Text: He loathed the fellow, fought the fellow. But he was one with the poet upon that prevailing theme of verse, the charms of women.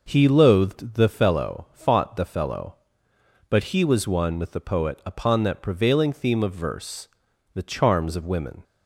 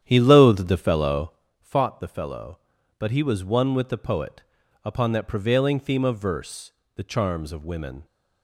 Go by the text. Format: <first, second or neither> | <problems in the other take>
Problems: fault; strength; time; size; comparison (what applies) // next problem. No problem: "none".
first | starts louder than the rest; strong; until 1.5 s; 9.5 dB // pauses between "poet" and "upon"; at 4.4 s; 0.42 s long